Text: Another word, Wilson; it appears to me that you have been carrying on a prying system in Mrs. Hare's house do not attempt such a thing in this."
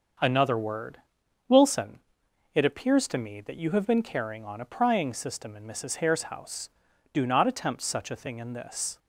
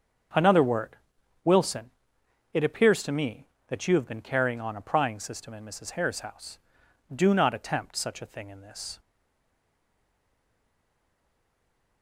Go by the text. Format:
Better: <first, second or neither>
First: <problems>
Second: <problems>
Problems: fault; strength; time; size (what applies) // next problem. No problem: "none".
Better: first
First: starts louder than the rest; until 1.6 s; 6.5 dB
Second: starts louder than the rest; until 1.8 s; 7 dB // stays silent after the last word; strong; from 8.9 s on; 3.1 s long